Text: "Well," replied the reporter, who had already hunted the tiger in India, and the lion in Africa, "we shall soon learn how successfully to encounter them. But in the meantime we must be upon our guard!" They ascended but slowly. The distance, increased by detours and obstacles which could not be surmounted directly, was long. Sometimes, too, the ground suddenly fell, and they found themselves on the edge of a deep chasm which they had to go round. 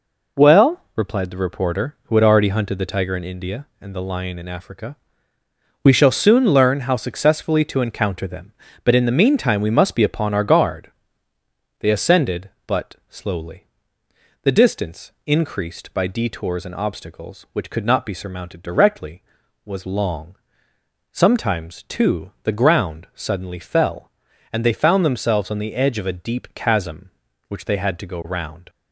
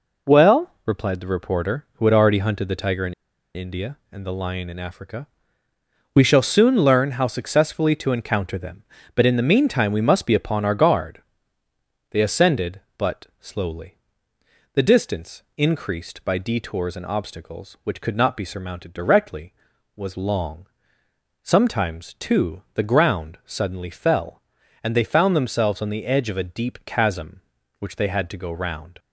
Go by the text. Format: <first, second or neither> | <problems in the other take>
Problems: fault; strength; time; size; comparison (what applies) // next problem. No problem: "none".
first | pauses between "in" and "India"; at 3.1 s; 0.41 s long